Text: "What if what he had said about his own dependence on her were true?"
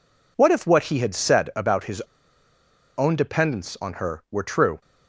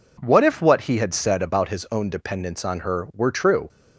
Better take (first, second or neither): second